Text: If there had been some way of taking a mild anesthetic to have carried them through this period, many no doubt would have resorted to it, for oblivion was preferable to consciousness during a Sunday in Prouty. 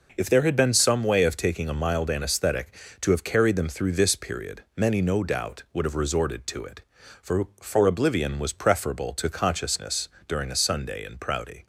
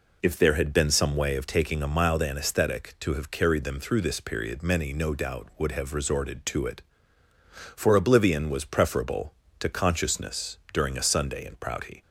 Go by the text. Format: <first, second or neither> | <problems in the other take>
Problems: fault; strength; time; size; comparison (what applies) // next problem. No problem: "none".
second | says "for" twice; at 7.5 s // pauses between "consciousness" and "during"; slight; at 10.0 s; 0.18 s long